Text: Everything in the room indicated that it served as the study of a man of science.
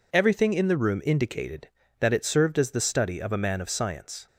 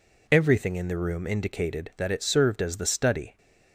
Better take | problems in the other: first | stops before "of a man of science"; at 3.3 s

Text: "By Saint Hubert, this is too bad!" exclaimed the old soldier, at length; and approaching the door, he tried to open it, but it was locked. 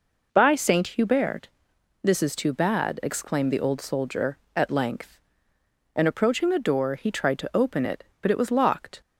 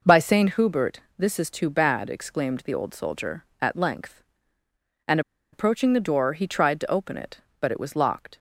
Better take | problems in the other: first | pauses between "and" and "approaching"; slight; at 5.2 s; 0.32 s long

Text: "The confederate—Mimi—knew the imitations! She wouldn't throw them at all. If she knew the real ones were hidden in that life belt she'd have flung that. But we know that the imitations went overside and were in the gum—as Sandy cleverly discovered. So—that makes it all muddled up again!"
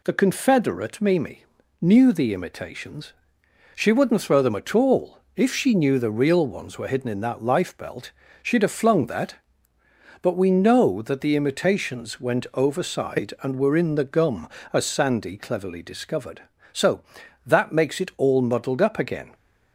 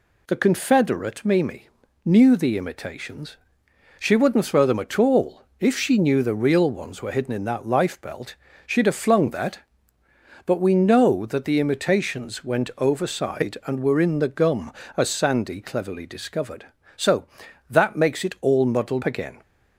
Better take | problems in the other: first | pauses between "belt" and "she'd"; slight; at 8.3 s; 0.30 s long; slight in the first // skips "up"; at 19.0 s

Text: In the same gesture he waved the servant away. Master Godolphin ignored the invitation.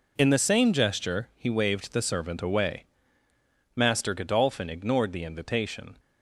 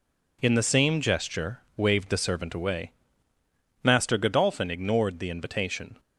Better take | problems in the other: first | skips "he"; at 1.6 s

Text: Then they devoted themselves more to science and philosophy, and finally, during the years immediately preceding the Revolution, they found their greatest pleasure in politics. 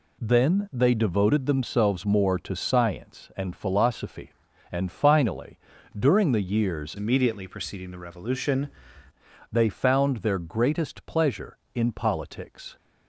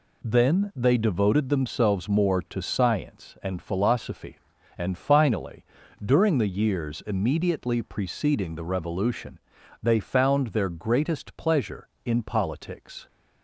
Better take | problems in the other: second | changes voice from "immediately" to "Revolution"; from 6.9 to 8.6 s; 1.7 s long

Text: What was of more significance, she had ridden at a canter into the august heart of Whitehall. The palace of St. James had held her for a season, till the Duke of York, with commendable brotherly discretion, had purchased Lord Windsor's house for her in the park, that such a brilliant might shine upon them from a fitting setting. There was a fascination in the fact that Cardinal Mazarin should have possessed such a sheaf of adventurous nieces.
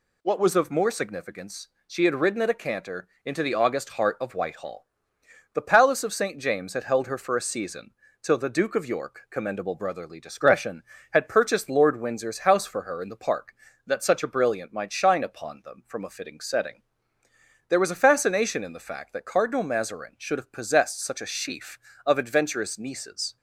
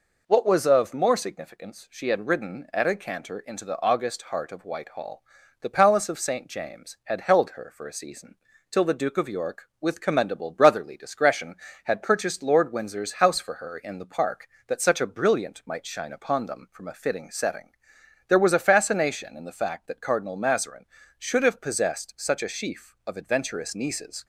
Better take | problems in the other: second | pauses between "canter" and "into"; slight; at 3.0 s; 0.16 s long // skips "with"; at 9.2 s

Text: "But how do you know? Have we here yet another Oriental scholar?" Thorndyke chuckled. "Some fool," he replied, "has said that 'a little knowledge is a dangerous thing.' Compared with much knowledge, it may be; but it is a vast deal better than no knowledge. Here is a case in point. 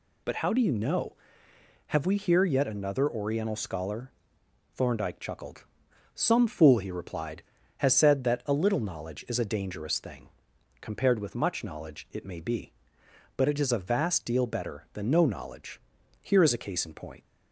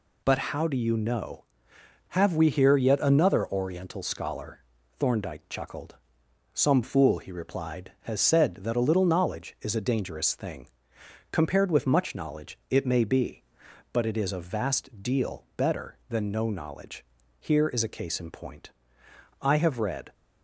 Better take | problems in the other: first | goes on to say "I have read"; noticeable; from 19.4 s on; 0.72 s long

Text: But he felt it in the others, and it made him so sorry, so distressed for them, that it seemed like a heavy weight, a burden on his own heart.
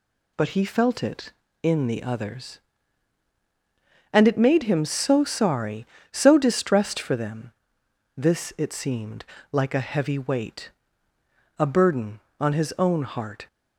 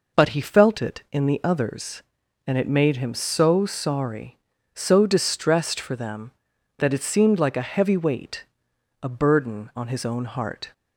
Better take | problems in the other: second | says "this" for "that"; at 8.1 s // pauses between "seemed" and "like"; slight; at 9.2 s; 0.26 s long

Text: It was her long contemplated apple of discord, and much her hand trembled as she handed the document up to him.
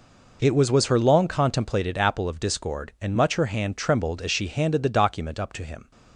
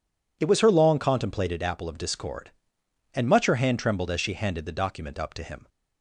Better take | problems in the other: second | says "was" twice; at 0.7 s

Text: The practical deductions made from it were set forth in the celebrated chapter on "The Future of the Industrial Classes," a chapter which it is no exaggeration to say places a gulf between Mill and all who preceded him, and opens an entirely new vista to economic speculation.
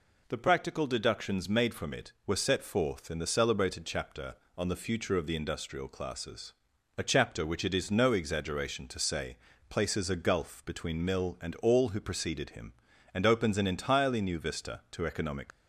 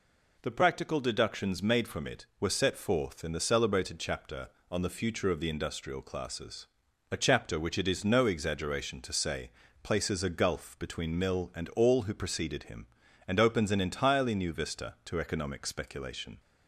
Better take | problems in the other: second | pauses between "say" and "places"; slight; at 9.3 s; 0.32 s long; slight in the second // stops before "speculation"; at 15.5 s

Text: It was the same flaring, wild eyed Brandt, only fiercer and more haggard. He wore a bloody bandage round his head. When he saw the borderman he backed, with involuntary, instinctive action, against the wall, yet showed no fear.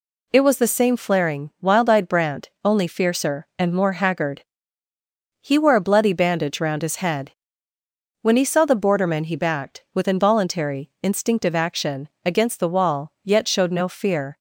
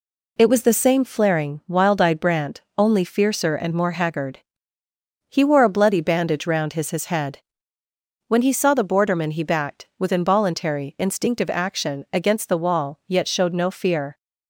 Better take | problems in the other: first | says "his" twice; at 6.9 s

